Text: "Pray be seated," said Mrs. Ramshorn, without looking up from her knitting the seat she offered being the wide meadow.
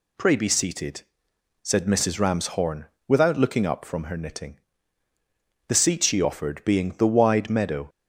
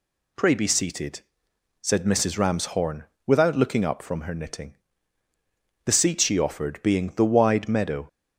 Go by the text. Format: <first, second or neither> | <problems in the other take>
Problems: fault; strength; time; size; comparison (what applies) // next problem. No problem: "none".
neither | pauses between "knitting" and "the"; the same in both